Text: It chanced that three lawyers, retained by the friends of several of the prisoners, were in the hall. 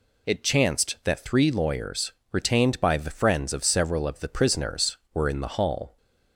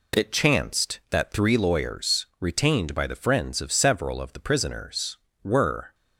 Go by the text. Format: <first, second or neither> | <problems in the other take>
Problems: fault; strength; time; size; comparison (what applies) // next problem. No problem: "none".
first | stops before "in the hall"; at 5.9 s